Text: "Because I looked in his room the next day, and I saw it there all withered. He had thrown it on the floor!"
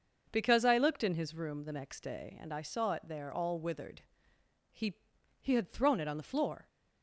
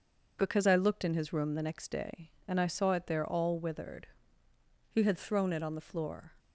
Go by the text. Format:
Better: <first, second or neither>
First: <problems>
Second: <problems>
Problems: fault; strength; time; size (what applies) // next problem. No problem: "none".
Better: second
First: says "He" twice; at 5.3 s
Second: none